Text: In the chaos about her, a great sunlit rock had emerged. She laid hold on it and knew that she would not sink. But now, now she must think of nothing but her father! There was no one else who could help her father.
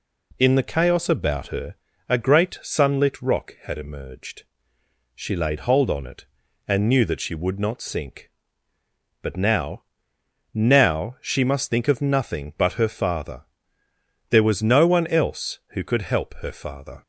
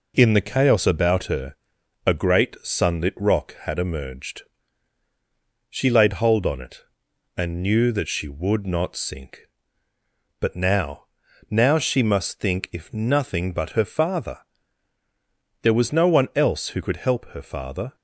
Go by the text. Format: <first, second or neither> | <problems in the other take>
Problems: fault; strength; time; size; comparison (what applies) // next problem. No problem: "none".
first | says "if" for "of"; at 12.7 s